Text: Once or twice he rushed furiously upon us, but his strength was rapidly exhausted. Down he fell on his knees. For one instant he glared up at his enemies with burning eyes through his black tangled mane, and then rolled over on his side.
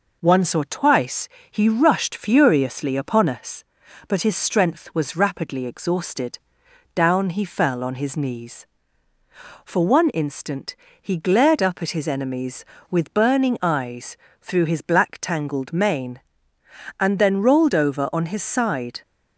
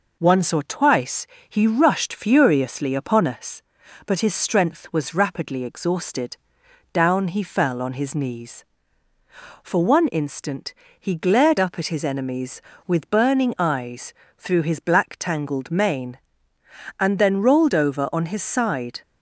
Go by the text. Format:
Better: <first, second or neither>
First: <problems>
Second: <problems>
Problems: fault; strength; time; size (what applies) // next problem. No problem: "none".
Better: neither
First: pauses between "twice" and "he"; slight; at 1.2 s; 0.20 s long // pauses between "instant" and "he"; slight; at 10.7 s; 0.26 s long // pauses between "eyes" and "through"; slight; at 14.1 s; 0.26 s long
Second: pauses between "twice" and "he"; slight; at 1.2 s; 0.20 s long // pauses between "instant" and "he"; slight; at 10.7 s; 0.26 s long // pauses between "eyes" and "through"; slight; at 14.1 s; 0.26 s long